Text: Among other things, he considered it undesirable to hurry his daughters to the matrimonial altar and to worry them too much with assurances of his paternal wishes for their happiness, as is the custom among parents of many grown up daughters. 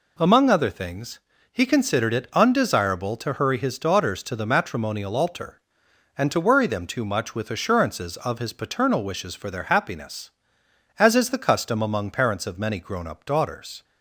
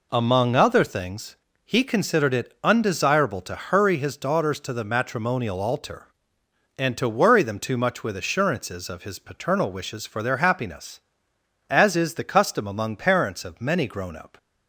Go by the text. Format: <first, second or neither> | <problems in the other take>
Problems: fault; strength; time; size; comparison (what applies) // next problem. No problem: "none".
first | stops before "daughters"; at 14.3 s